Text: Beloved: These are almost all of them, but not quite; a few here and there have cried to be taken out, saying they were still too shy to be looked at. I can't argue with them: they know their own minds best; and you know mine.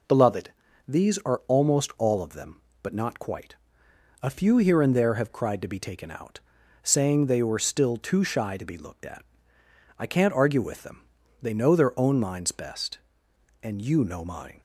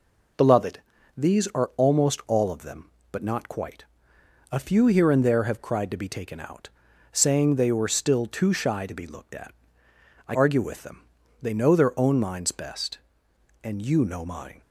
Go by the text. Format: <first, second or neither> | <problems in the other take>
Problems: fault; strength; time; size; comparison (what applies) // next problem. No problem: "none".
first | skips "can't"; at 10.3 s